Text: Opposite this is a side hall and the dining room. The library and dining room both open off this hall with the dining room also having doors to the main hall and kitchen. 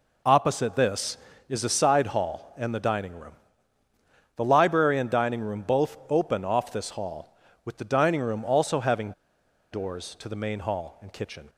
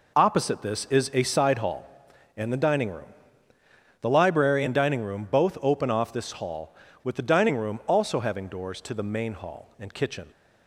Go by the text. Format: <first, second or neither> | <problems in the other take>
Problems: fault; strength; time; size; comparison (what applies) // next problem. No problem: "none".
second | pauses between "having" and "doors"; noticeable; at 9.1 s; 0.60 s long